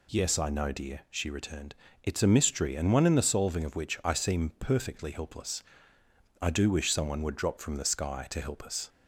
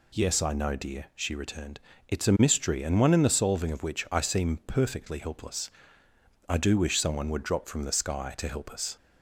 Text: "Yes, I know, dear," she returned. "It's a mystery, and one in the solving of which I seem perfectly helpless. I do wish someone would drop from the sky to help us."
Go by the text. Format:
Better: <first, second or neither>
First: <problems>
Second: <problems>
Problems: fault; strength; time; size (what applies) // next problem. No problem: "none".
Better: neither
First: none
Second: none